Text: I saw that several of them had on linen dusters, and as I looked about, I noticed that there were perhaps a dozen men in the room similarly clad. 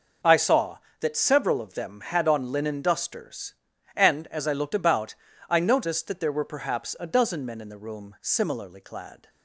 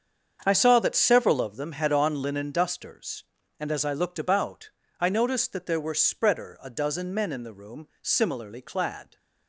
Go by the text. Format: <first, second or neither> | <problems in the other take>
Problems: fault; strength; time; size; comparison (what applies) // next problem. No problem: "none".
first | starts louder than the rest; strong; until 1.4 s; 7 dB // says "spreader" for "perhaps"; at 5.9 s